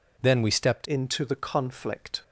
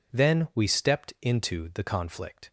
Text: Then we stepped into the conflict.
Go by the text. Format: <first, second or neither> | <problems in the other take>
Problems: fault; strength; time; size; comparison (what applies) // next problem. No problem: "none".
second | changes voice at "into"; from 0.8 s on; 1.4 s long